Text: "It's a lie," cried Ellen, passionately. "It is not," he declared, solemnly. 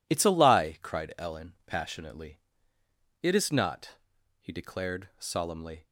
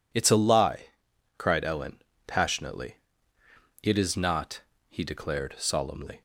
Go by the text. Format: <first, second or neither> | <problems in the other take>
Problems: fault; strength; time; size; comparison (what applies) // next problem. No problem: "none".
neither | none